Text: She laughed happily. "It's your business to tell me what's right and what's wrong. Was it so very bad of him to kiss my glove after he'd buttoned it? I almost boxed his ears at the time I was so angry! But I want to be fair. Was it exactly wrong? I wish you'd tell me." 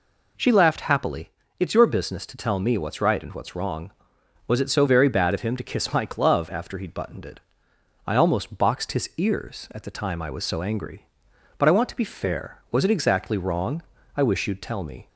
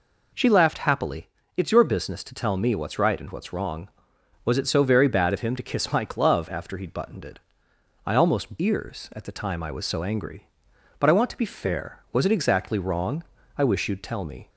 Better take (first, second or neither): first